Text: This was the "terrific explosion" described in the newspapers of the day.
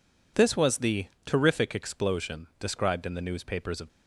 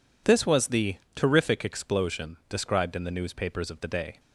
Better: second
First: pauses between "the" and "terrific"; slight; at 1.0 s; 0.20 s long // stops before "the day"; at 3.8 s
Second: pauses between "the" and "terrific"; slight; at 0.9 s; 0.20 s long

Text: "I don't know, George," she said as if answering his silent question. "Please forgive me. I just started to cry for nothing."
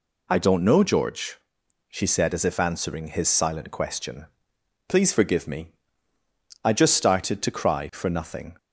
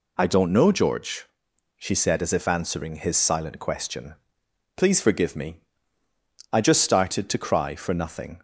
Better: neither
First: none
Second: none

